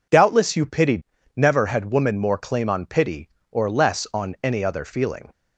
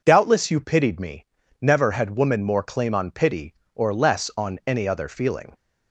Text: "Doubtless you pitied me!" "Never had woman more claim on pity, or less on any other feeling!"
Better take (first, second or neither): second